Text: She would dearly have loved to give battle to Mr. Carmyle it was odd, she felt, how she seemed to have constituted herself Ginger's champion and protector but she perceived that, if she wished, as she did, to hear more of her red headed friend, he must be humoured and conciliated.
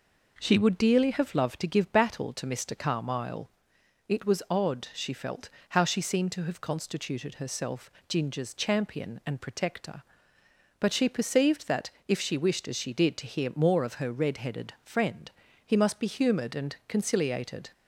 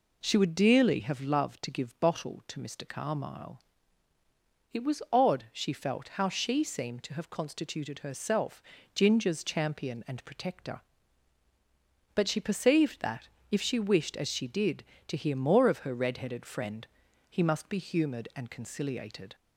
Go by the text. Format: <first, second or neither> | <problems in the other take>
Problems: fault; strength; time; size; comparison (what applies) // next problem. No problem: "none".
first | says "bottle" for "battle"; at 1.9 s // pauses between "Carmyle" and "it"; at 3.5 s; 1.1 s long; noticeable in the first // pauses between "herself" and "Ginger's"; slight; at 8.6 s; 0.32 s long; slight in the first